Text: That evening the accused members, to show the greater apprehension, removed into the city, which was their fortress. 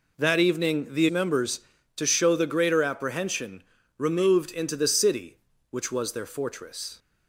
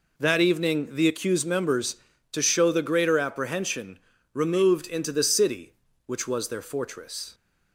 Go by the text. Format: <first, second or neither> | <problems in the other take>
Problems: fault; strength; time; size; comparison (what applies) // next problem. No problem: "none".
second | skips "accused"; at 1.0 s